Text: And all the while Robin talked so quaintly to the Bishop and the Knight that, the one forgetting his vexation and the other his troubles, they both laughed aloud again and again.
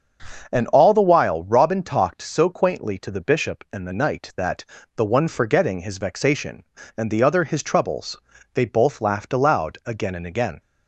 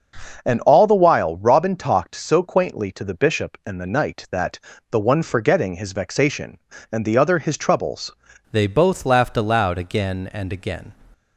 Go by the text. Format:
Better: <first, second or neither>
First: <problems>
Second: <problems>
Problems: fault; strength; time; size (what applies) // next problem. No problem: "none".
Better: first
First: starts louder than the rest; until 1.5 s; 6.5 dB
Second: starts louder than the rest; noticeable; until 1.4 s; 6 dB // changes voice at "they"; from 8.5 s on; 2.4 s long